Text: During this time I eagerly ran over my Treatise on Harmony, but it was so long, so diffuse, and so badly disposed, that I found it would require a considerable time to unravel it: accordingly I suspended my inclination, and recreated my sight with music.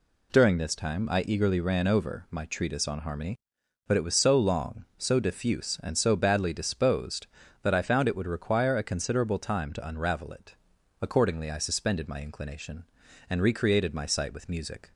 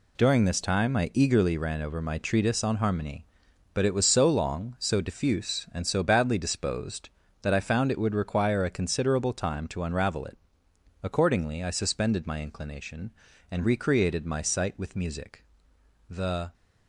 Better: first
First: none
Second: goes on to say "The"; slight; from 16.0 s on; 0.44 s long

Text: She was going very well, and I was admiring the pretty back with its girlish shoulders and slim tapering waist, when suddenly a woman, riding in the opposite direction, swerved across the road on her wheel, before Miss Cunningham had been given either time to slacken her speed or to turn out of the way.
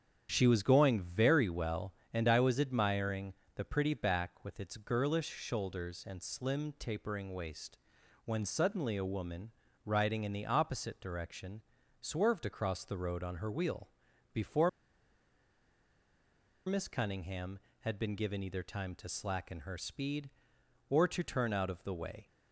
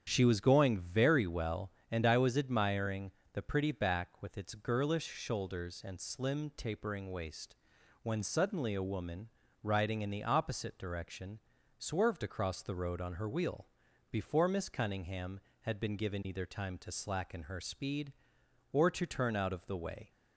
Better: second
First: starts louder than the rest; strong; until 1.3 s; 8.5 dB // pauses between "admiring" and "the"; slight; at 3.3 s; 0.24 s long // pauses between "before" and "Miss"; strong; at 14.6 s; 1.9 s long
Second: starts louder than the rest; strong; until 1.1 s; 8 dB // pauses between "admiring" and "the"; slight; at 3.0 s; 0.24 s long

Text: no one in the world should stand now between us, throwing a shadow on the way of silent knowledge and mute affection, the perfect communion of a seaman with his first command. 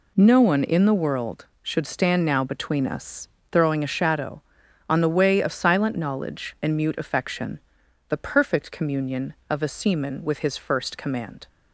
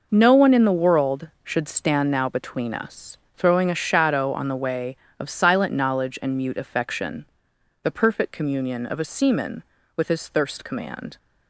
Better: first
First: none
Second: says "thirst" for "first"; at 10.2 s

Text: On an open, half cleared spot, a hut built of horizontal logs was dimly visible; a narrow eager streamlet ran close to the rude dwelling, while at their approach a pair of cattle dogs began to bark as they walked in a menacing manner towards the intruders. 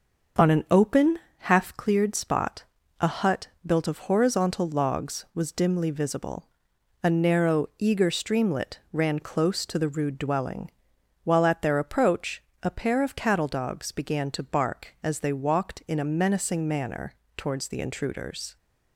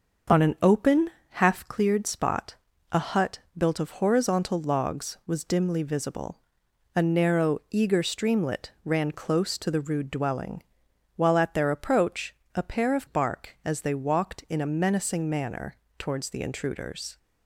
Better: first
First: starts louder than the rest; until 1.6 s; 6.5 dB // pauses between "hut" and "built"; slight; at 3.4 s; 0.18 s long // pauses between "approach" and "a"; slight; at 12.4 s; 0.20 s long // pauses between "manner" and "towards"; slight; at 17.1 s; 0.24 s long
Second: starts louder than the rest; until 1.5 s; 6.5 dB // pauses between "hut" and "built"; slight; at 3.3 s; 0.18 s long // pauses between "approach" and "a"; slight; at 12.3 s; 0.20 s long // skips "cattle dogs began to"; at 13.0 s // pauses between "manner" and "towards"; slight; at 15.7 s; 0.24 s long

